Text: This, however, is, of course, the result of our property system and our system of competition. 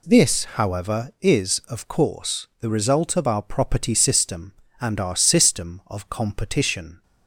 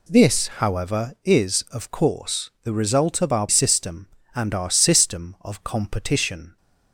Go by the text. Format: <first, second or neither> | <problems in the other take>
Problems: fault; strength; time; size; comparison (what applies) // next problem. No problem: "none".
first | skips "property"; at 3.4 s